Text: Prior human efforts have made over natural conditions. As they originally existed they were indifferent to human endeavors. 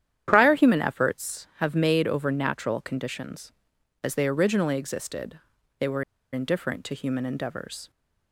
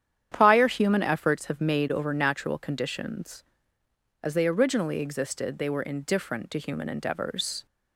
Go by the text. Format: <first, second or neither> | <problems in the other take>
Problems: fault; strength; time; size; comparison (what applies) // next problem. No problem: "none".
second | starts louder than the rest; strong; until 1.2 s; 10 dB; strong in the second // pauses between "existed" and "they"; at 5.3 s; 0.40 s long // pauses between "were" and "indifferent"; slight; at 6.0 s; 0.29 s long